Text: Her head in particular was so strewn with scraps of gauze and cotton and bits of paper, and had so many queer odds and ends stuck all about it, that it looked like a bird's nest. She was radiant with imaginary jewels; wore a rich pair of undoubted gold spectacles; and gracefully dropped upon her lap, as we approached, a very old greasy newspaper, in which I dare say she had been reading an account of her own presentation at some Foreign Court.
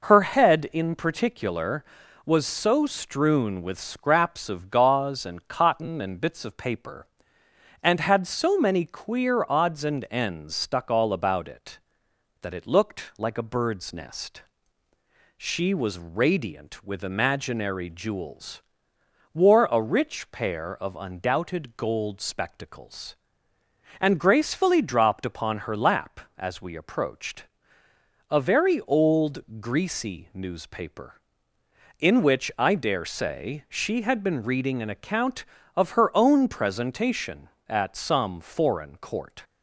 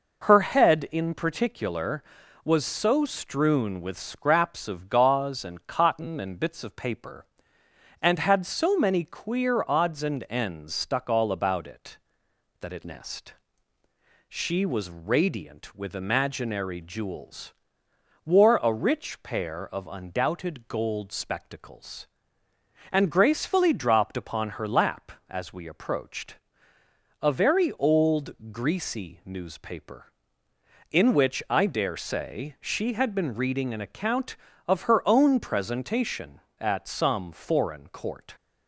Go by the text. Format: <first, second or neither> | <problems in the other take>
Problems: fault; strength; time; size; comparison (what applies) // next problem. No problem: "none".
first | skips "looked like a bird's"; at 12.8 s